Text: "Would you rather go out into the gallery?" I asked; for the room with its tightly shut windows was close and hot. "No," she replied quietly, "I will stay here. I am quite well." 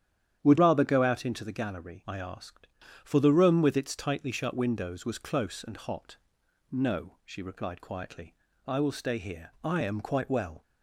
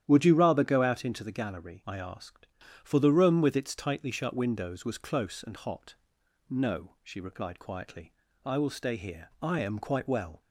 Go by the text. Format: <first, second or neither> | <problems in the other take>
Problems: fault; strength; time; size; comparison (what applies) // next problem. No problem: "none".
second | starts louder than the rest; strong; until 1.4 s; 10 dB; strong in the second // skips "you"; at 0.5 s